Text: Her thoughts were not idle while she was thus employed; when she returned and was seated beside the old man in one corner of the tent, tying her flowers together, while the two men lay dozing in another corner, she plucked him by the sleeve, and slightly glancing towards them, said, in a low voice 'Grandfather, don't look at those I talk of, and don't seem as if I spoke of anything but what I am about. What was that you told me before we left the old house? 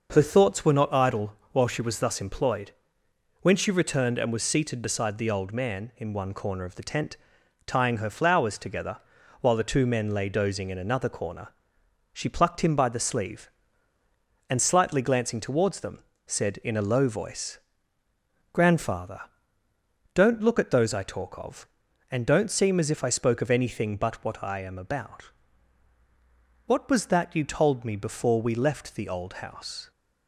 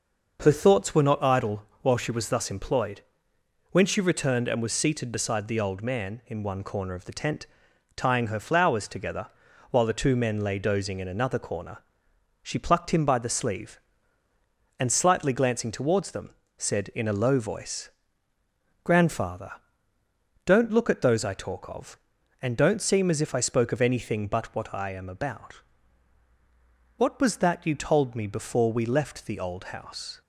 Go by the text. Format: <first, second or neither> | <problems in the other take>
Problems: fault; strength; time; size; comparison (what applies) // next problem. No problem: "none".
neither | starts louder than the rest; noticeable; the same in both // pauses between "idle" and "while"; slight; the same in both // pauses between "voice" and "Grandfather"; noticeable; the same in both